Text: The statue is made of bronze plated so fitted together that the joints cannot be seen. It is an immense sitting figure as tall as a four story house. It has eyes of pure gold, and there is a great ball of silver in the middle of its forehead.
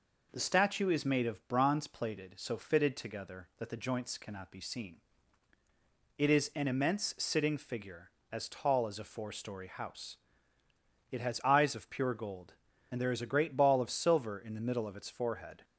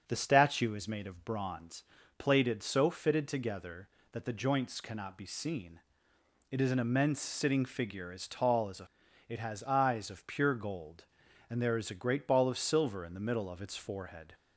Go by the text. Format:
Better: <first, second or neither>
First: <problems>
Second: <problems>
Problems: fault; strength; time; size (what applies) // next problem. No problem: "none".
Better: first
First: none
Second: starts louder than the rest; until 1.0 s; 6 dB // pauses between "bronze" and "plated"; slight; at 1.8 s; 0.36 s long // skips "four story house"; at 9.0 s